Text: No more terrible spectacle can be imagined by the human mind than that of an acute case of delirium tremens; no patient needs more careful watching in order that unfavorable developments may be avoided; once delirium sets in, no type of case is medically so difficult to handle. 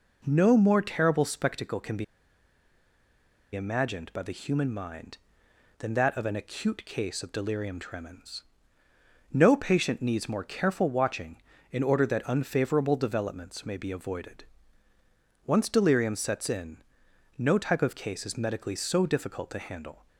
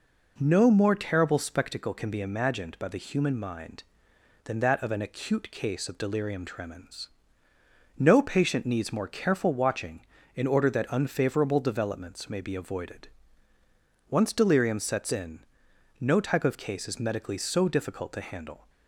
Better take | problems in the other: second | pauses between "be" and "imagined"; strong; at 2.0 s; 1.5 s long

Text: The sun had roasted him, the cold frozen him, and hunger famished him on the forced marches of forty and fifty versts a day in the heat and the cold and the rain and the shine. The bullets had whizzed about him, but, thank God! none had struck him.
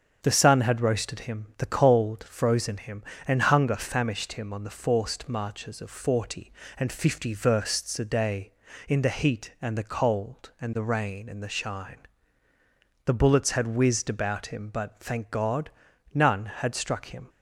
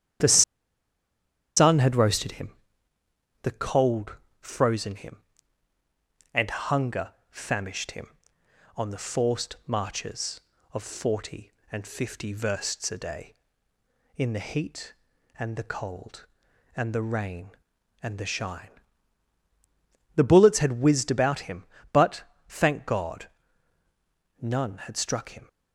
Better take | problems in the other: first | starts louder than the rest; strong; until 2.3 s; 10 dB; strong in the first // pauses between "The" and "sun"; at 0.4 s; 1.1 s long // pauses between "cold" and "frozen"; slight; at 4.1 s; 0.22 s long // pauses between "hunger" and "famished"; slight; at 7.0 s; 0.22 s long

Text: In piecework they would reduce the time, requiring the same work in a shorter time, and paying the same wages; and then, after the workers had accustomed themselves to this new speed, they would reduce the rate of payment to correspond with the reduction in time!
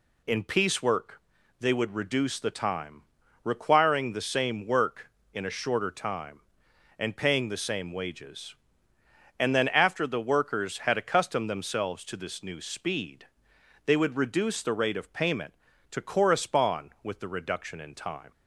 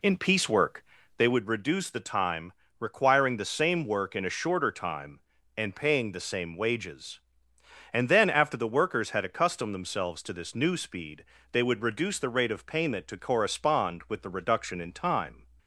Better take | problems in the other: first | starts louder than the rest; slight; until 1.4 s; 2 dB // pauses between "piecework" and "they"; slight; at 0.8 s; 0.36 s long; also in the first

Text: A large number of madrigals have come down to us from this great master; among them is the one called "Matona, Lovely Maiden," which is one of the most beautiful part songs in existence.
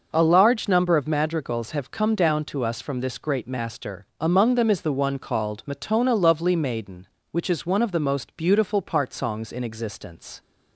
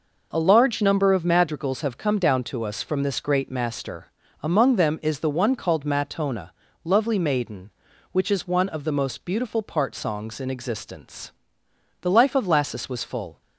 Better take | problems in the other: first | goes on to say "The life of Lassus was full"; from 12.0 s on; 1.3 s long

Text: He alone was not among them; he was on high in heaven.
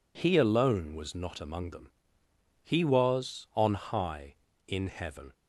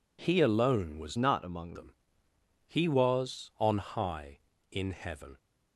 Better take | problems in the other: first | changes voice from "not" to "among"; from 1.1 to 1.7 s; 0.6 s long

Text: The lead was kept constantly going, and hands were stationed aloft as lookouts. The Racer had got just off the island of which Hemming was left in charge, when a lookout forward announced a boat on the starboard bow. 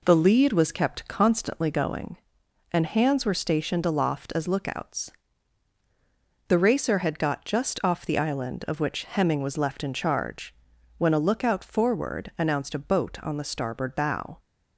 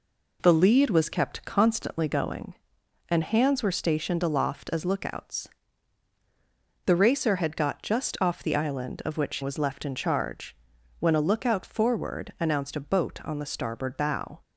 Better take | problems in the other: first | skips "Hemming"; at 9.4 s

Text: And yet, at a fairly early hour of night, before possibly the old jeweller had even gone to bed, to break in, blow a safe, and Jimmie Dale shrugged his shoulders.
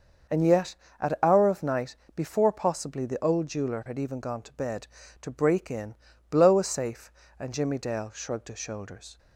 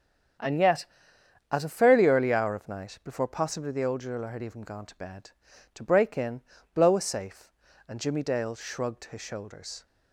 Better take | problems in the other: second | starts louder than the rest; until 1.5 s; 6.5 dB; strong in the second // skips "a fairly early"; at 1.2 s

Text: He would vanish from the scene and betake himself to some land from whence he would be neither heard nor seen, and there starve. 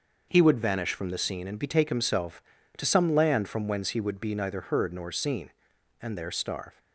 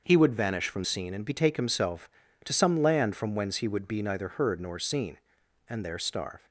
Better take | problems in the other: first | starts louder than the rest; until 1.0 s; 6 dB; also in the first // skips "the"; at 0.8 s

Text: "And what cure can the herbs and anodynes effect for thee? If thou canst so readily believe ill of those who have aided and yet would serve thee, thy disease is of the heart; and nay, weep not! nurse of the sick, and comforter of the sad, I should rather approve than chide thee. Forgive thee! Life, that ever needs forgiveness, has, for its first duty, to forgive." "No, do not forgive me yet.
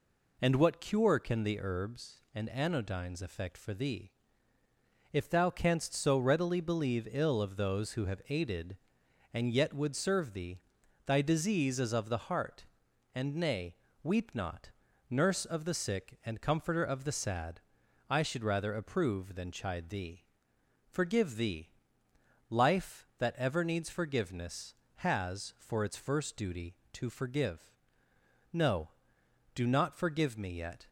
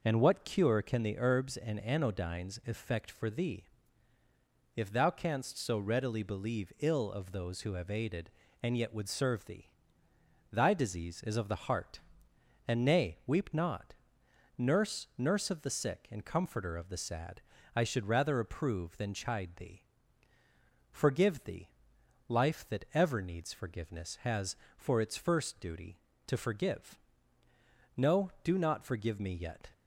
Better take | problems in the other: first | says "nurse" twice; at 15.1 s

